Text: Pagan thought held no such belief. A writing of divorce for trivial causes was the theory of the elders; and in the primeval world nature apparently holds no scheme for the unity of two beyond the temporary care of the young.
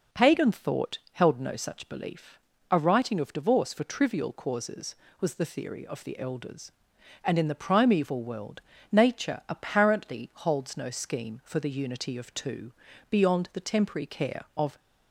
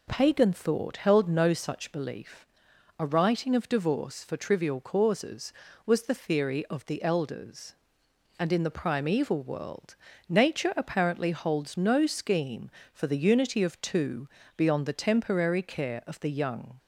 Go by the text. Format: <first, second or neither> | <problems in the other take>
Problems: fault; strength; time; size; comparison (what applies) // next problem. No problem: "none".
second | pauses between "world" and "nature"; slight; at 8.6 s; 0.30 s long; slight in the second // pauses between "two" and "beyond"; at 12.7 s; 0.38 s long; slight in the second // stops before "the young"; at 14.7 s